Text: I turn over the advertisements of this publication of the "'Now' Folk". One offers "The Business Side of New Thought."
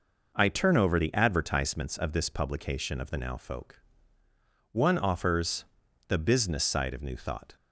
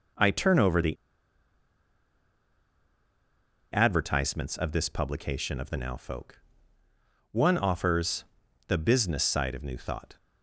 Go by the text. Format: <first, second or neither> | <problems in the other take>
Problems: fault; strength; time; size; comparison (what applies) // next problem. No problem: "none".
first | pauses between "the" and "advertisements"; strong; at 0.9 s; 2.7 s long // pauses between "offers" and "The"; at 8.2 s; 0.44 s long; also in the first